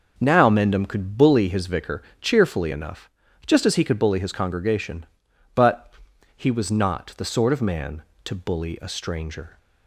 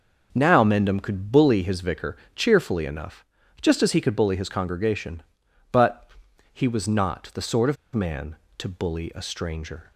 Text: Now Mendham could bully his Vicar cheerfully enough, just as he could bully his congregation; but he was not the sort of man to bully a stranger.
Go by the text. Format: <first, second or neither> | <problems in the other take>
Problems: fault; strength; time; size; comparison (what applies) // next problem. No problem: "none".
first | pauses between "Vicar" and "cheerfully"; slight; at 2.1 s; 0.20 s long; slight in the first // pauses between "but" and "he"; at 6.0 s; 0.44 s long; also in the first // pauses between "of" and "man"; slight; at 7.7 s; 0.18 s long